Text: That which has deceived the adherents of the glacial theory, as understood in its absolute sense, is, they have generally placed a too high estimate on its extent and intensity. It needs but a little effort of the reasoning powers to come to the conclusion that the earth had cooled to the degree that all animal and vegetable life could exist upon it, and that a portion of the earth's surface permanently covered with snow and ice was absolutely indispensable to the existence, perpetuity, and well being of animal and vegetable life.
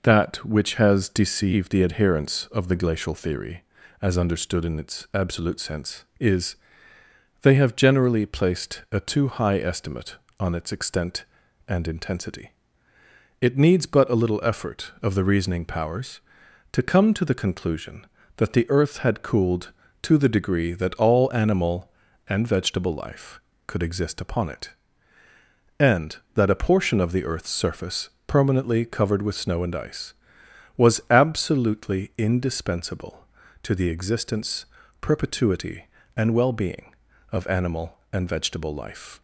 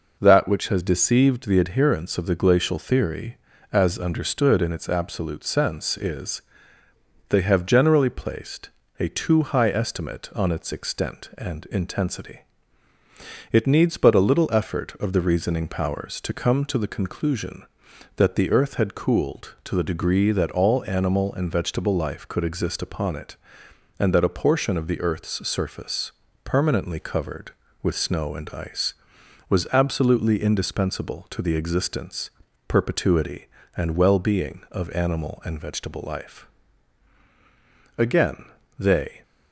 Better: first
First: pauses between "surface" and "permanently"; slight; at 28.1 s; 0.16 s long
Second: pauses between "placed" and "a"; slight; at 8.6 s; 0.28 s long // pauses between "surface" and "permanently"; slight; at 26.1 s; 0.32 s long // goes on to say "Again they"; noticeable; from 37.9 s on; 1.2 s long

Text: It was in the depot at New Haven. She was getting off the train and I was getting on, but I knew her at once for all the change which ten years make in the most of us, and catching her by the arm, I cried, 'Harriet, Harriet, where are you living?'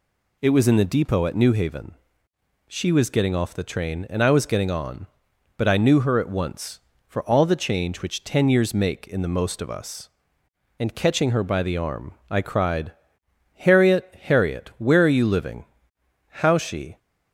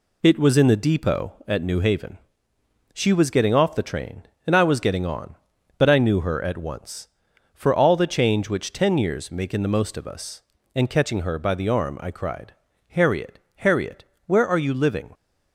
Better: second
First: goes on to say "How she"; noticeable; from 16.2 s on; 0.70 s long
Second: none

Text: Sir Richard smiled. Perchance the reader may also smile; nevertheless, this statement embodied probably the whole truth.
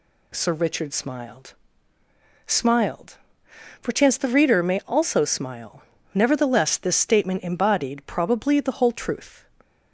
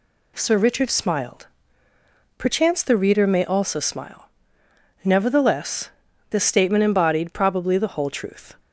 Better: second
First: says "smiled" twice; at 2.4 s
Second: none

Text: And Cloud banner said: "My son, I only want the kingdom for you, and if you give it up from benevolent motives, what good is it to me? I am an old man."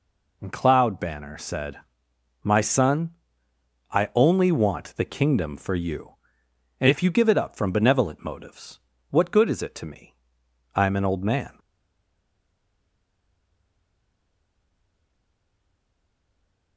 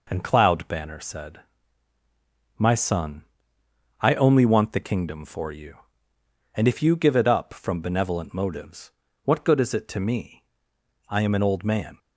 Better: second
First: stays silent after the last word; strong; from 11.5 s on; 5.2 s long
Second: none

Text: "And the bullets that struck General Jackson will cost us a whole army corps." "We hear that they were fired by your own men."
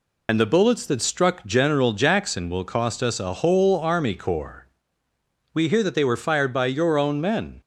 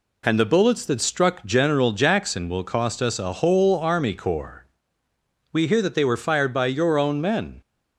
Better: second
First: loses the start of "And"; at 0.2 s; 50 ms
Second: none

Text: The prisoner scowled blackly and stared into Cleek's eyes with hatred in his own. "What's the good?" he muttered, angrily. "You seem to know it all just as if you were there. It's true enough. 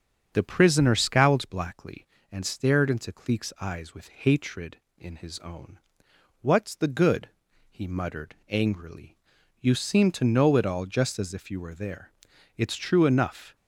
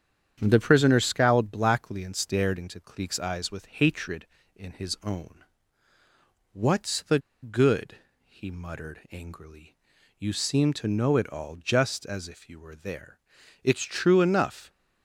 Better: first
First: starts louder than the rest; strong; until 1.3 s; 7 dB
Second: starts louder than the rest; strong; until 1.4 s; 8.5 dB // pauses between "the" and "good"; slight; at 7.1 s; 0.24 s long

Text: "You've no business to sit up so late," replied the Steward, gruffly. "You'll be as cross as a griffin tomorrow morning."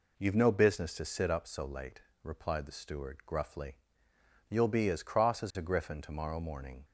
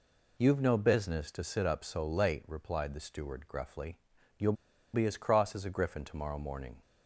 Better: first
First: none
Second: pauses between "You'll" and "be"; at 4.5 s; 0.40 s long

